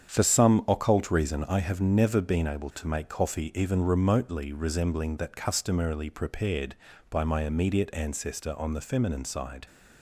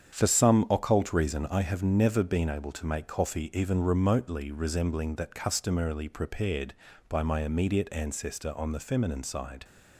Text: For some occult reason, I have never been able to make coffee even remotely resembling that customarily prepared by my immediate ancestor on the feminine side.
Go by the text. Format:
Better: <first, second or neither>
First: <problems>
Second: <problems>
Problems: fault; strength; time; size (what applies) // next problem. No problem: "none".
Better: neither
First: starts louder than the rest; strong; until 1.1 s; 8 dB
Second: starts louder than the rest; strong; until 1.1 s; 7.5 dB